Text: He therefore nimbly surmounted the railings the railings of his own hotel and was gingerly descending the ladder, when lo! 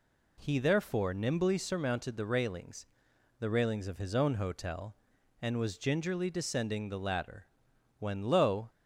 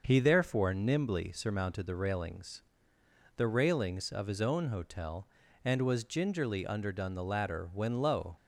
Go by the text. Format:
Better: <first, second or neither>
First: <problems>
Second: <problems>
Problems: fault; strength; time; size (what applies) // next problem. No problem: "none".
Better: first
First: pauses between "railings" and "the"; noticeable; at 2.8 s; 0.52 s long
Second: starts louder than the rest; until 1.0 s; 6.5 dB // pauses between "railings" and "the"; noticeable; at 2.6 s; 0.76 s long // says "underdone" for "descending"; at 6.6 s